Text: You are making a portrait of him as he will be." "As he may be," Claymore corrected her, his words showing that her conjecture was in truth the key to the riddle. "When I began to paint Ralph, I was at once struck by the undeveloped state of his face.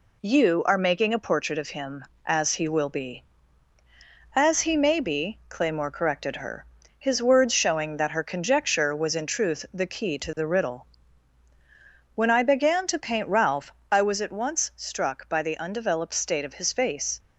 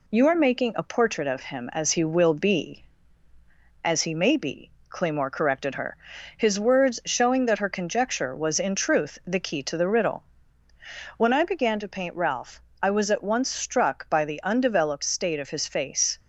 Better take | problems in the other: neither | none

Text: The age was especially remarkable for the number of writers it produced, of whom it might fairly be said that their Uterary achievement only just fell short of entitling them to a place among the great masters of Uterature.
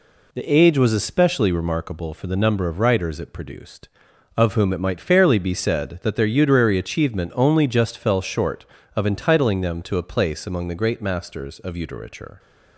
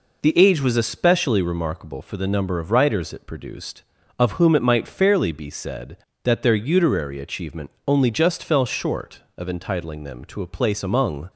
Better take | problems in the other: first | pauses between "achievement" and "only"; slight; at 7.7 s; 0.18 s long // stops before "the great masters of Uterature"; at 11.3 s

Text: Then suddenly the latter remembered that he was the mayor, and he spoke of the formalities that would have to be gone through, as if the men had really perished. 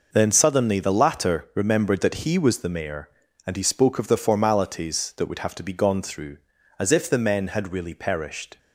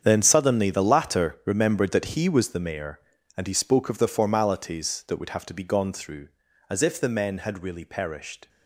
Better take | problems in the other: first | gets quieter; strong; throughout; 12.5 dB

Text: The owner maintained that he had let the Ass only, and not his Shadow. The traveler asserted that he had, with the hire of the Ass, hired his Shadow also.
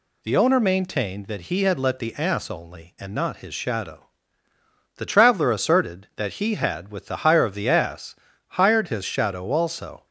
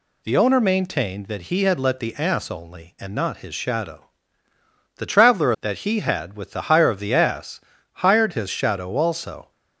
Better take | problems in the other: first | skips "asserted"; at 5.5 s

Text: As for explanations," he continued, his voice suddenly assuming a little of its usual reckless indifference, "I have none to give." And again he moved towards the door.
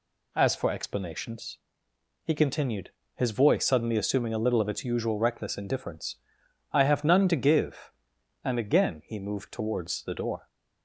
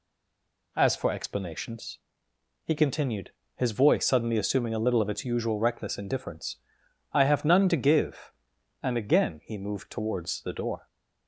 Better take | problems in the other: first | stays silent before the first word; slight; until 0.7 s; 0.7 s long

